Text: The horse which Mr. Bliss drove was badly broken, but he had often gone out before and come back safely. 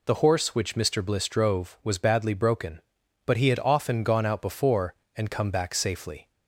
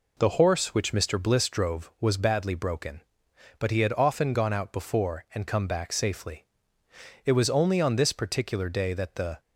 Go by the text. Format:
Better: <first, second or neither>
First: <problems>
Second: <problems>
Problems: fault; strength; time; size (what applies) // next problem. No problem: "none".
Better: first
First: none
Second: goes on to say "It was only on this particular day that the"; strong; from 7.2 s on; 2.1 s long